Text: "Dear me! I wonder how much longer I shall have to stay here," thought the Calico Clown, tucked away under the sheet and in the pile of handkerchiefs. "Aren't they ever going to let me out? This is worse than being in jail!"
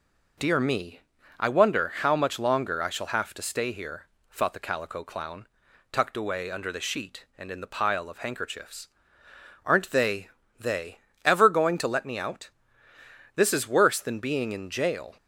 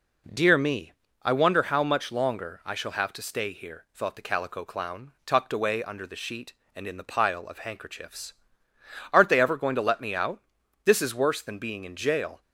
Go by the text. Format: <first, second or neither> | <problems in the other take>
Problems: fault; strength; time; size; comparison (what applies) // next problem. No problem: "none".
second | says "they" twice; at 10.5 s